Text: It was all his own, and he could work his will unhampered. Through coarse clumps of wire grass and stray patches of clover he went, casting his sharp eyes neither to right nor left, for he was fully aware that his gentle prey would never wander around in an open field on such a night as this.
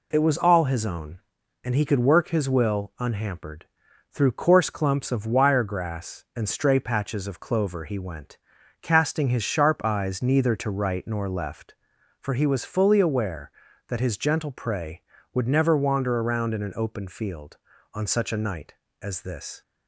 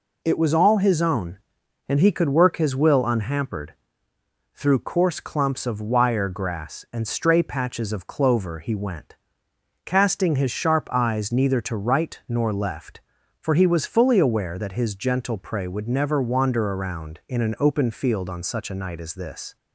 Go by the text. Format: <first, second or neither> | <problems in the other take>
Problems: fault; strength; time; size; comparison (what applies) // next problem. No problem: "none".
neither | none